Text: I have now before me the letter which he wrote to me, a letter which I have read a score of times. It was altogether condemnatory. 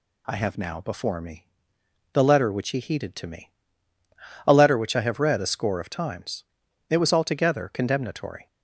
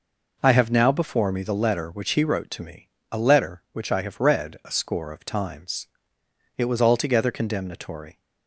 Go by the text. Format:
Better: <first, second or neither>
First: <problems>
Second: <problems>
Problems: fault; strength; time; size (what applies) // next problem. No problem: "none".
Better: second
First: pauses between "me" and "the"; noticeable; at 1.4 s; 0.68 s long // says "heeded" for "wrote"; at 2.7 s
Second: none